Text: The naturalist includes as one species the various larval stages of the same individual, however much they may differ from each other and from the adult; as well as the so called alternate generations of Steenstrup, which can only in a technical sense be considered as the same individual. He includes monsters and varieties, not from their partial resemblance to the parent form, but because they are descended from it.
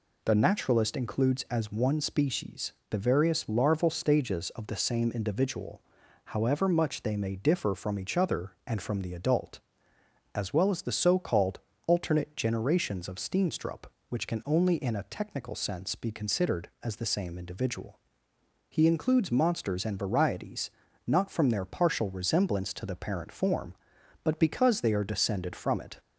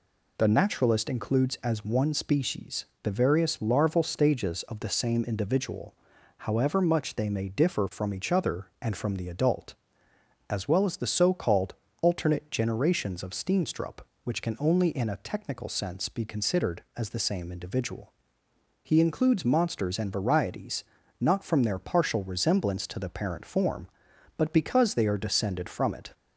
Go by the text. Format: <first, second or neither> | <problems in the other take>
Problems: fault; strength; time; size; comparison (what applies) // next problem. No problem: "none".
neither | pauses between "species" and "the"; slight; the same in both // pauses between "called" and "alternate"; slight; the same in both